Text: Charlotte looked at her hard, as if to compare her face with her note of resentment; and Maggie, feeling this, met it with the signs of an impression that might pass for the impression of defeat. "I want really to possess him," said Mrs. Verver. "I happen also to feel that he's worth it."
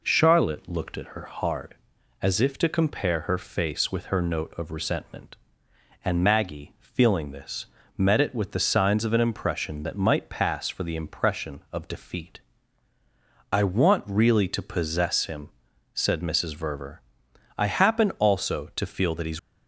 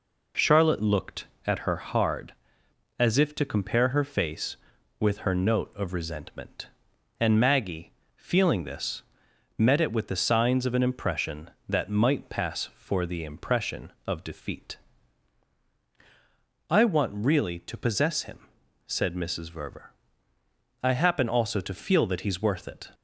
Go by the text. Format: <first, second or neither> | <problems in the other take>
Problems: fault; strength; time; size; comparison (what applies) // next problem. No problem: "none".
second | stops before "worth it"; at 19.3 s